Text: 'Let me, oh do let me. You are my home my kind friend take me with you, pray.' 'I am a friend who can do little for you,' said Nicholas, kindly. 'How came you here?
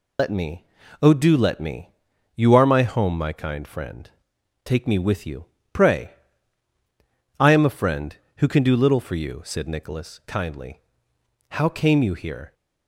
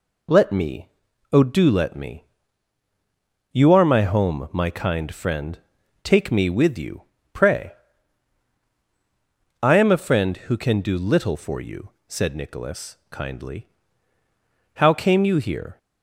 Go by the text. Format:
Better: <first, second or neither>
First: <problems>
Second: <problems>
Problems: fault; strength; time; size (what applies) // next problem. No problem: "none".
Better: second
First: loses the start of "Let"; at 0.1 s; 100 ms // pauses between "friend" and "take"; noticeable; at 4.0 s; 0.56 s long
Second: pauses between "friend" and "take"; noticeable; at 5.5 s; 0.46 s long